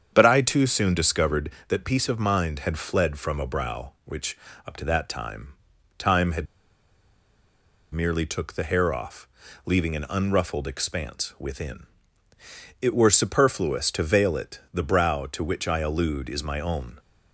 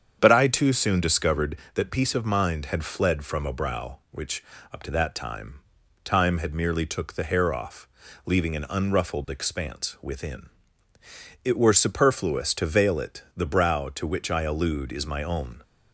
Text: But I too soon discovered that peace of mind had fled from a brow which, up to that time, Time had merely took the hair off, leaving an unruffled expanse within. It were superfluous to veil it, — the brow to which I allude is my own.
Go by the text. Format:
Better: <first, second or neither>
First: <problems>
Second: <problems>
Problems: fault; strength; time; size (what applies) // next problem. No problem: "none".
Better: second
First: starts louder than the rest; strong; until 1.1 s; 8 dB // pauses between "had" and "merely"; strong; at 6.4 s; 1.4 s long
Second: starts louder than the rest; strong; until 1.2 s; 8 dB